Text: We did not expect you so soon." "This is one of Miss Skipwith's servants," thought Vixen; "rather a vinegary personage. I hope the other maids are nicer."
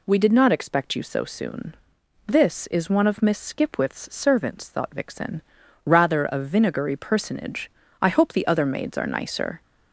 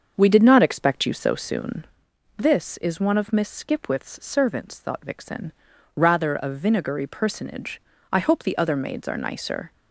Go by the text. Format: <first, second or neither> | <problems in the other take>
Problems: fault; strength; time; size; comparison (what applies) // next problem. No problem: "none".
first | starts louder than the rest; until 2.0 s; 6.5 dB